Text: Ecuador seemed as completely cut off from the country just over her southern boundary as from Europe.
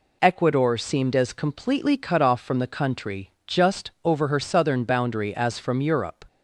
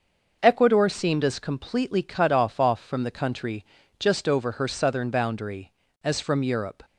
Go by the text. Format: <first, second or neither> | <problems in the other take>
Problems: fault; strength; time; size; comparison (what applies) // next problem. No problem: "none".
first | starts louder than the rest; until 1.4 s; 6 dB // says "off" twice; at 2.6 s // pauses between "country" and "just"; slight; at 3.6 s; 0.34 s long; slight in the first